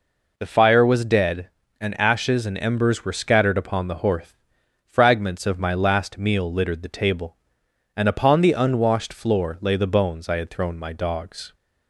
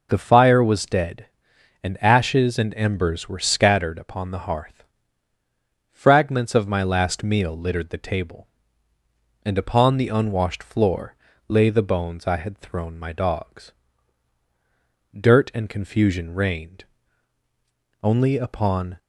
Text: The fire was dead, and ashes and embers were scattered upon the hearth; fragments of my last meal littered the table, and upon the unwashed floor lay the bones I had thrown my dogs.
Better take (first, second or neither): first